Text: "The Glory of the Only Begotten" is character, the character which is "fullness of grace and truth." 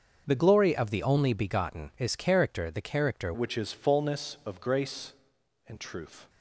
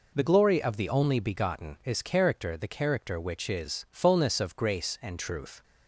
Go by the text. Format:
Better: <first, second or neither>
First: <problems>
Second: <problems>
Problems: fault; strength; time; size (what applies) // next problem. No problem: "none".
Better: second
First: starts louder than the rest; until 1.2 s; 6.5 dB // changes voice at "which"; from 3.3 s on; 2.9 s long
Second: none